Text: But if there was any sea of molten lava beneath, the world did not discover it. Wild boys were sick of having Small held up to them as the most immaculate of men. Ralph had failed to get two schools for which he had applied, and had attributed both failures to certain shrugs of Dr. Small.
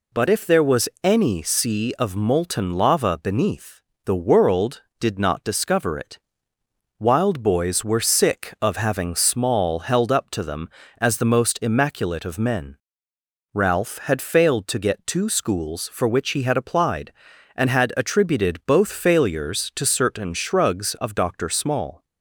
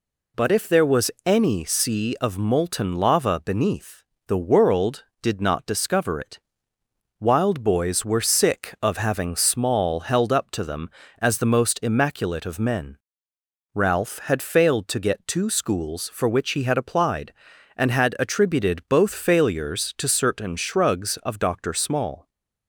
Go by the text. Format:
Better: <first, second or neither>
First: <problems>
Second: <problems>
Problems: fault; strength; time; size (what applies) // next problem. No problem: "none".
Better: neither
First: pauses between "was" and "any"; slight; at 0.8 s; 0.16 s long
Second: pauses between "was" and "any"; slight; at 1.1 s; 0.16 s long